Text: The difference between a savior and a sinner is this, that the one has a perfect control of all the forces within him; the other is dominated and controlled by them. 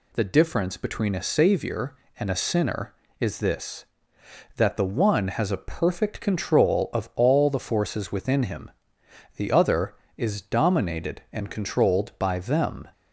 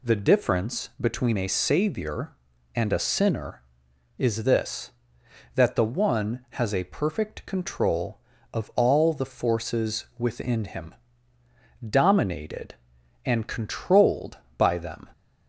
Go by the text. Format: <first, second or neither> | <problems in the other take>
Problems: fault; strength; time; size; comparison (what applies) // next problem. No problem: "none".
first | skips "the other is"; at 11.4 s